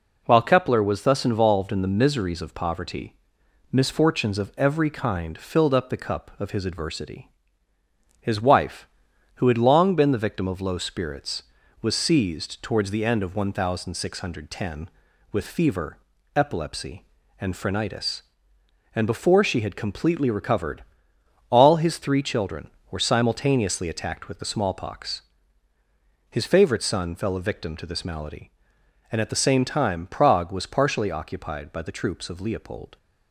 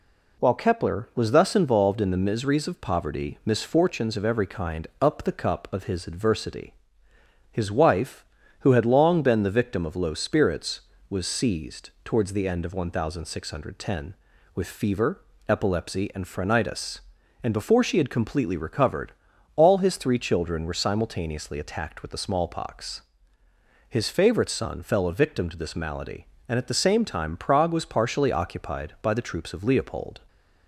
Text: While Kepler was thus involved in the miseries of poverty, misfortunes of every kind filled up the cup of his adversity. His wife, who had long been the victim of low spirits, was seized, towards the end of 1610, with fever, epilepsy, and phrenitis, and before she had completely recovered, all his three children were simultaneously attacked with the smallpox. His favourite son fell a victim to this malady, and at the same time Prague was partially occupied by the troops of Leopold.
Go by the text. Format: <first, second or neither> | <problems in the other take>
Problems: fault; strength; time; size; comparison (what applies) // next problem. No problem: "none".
first | skips "filled"; at 4.9 s